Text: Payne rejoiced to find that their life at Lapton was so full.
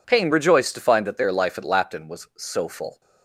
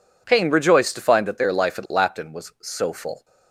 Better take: neither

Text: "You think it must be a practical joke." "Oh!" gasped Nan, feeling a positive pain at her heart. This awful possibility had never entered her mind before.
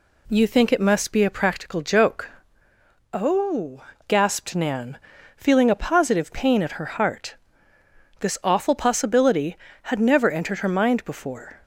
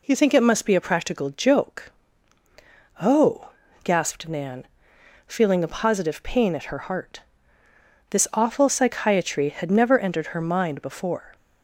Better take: first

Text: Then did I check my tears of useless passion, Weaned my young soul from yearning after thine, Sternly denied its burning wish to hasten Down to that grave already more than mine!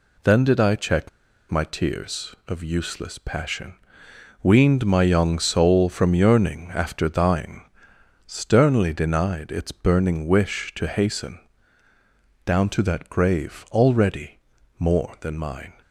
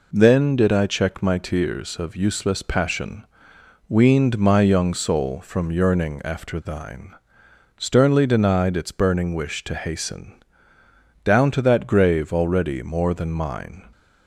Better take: second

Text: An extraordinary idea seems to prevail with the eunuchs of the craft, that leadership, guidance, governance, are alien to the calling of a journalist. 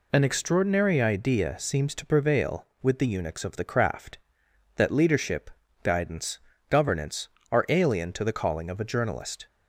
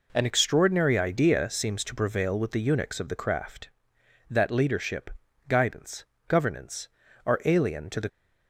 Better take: first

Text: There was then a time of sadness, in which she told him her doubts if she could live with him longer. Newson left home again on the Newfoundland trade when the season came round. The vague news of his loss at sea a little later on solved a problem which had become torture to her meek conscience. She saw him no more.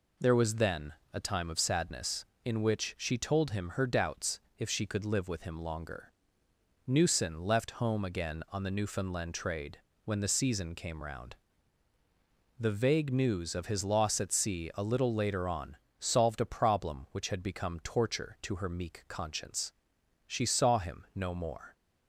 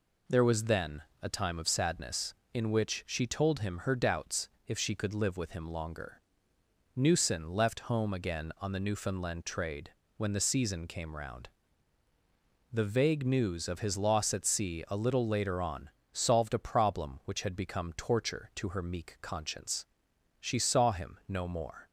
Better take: neither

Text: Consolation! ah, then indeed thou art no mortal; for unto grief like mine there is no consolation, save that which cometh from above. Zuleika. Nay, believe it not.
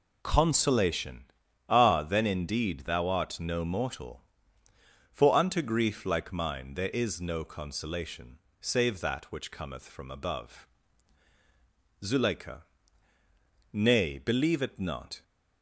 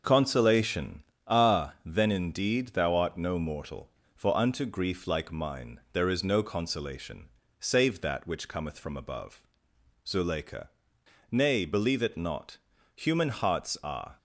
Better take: first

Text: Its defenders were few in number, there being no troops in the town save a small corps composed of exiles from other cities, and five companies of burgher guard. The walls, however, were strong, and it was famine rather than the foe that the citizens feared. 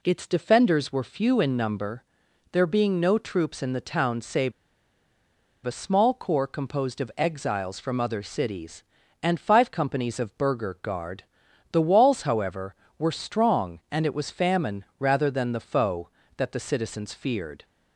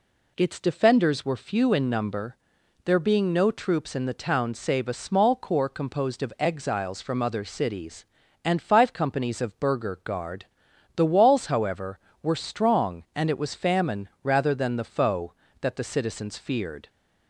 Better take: second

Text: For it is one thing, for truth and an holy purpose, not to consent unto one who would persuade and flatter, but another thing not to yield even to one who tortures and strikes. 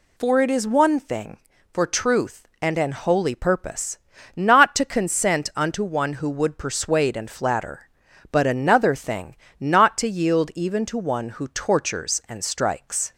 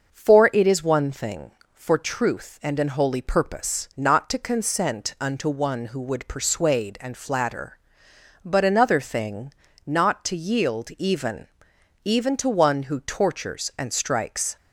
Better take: first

